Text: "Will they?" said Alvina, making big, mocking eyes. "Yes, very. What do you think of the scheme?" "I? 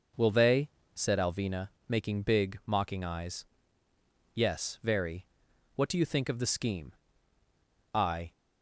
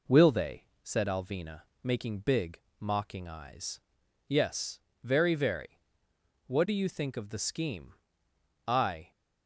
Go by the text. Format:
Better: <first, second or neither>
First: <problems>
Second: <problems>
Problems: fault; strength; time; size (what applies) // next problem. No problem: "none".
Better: first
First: none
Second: says "very" twice; at 5.3 s